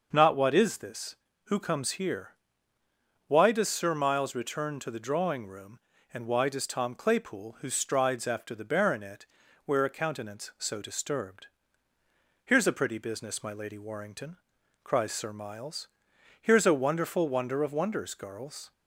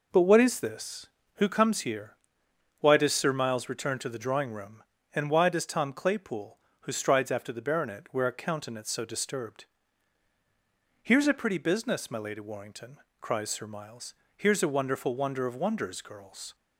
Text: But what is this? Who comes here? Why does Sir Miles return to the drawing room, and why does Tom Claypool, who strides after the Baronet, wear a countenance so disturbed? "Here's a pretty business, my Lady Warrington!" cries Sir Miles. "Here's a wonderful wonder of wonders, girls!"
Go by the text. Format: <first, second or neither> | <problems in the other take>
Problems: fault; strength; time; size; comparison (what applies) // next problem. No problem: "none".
second | says "Not" for "But"; at 0.1 s